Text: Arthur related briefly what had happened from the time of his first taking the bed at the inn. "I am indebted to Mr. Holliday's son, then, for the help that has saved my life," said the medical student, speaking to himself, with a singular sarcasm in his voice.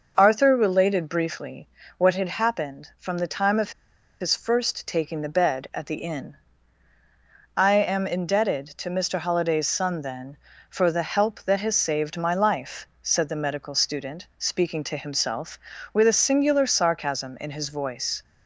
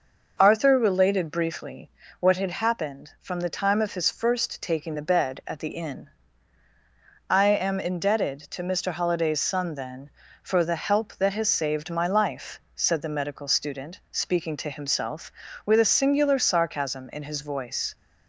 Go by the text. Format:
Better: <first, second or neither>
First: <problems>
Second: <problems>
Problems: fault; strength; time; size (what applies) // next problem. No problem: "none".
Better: second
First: pauses between "briefly" and "what"; slight; at 1.6 s; 0.30 s long // pauses between "of" and "his"; noticeable; at 3.7 s; 0.48 s long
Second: pauses between "briefly" and "what"; slight; at 1.9 s; 0.30 s long